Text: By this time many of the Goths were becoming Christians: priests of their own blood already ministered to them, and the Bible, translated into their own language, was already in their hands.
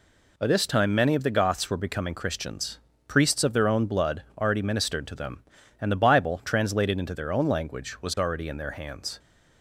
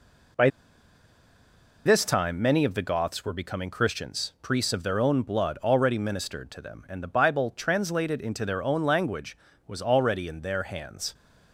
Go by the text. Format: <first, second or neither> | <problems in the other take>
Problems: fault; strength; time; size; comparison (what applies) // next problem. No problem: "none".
first | pauses between "By" and "this"; strong; at 0.4 s; 1.3 s long